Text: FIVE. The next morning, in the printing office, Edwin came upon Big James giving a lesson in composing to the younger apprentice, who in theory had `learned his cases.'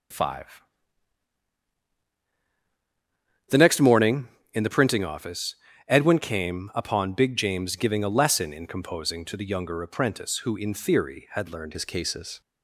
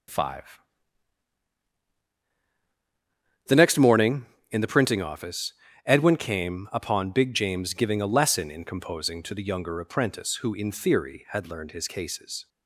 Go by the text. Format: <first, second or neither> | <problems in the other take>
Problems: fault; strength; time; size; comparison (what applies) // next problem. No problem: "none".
second | starts louder than the rest; until 4.0 s; 7 dB; also in the second // changes voice at "his"; from 11.7 s on; 0.7 s long